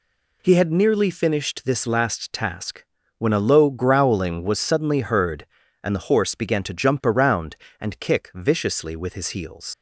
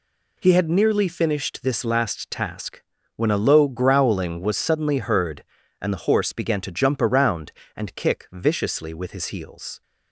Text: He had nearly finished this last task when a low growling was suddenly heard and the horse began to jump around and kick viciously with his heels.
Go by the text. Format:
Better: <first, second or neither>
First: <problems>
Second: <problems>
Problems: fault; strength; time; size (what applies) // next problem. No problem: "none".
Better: second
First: pauses between "task" and "when"; slight; at 2.8 s; 0.34 s long // leaves "heels" unfinished; at 9.7 s; 100 ms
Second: pauses between "task" and "when"; slight; at 2.8 s; 0.34 s long